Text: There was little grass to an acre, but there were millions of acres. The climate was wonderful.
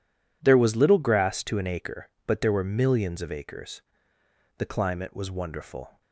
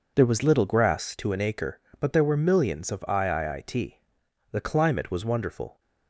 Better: first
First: none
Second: says "iiit" for "acres"; at 3.0 s

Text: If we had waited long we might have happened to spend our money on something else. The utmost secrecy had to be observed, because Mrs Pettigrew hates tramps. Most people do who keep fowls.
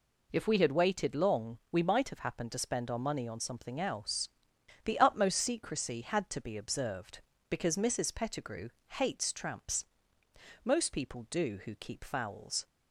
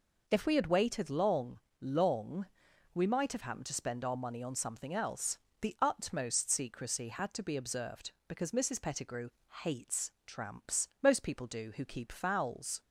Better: first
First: pauses between "Pettigrew" and "hates"; slight; at 8.6 s; 0.24 s long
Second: says "long" twice; at 1.8 s // pauses between "Pettigrew" and "hates"; slight; at 9.2 s; 0.35 s long

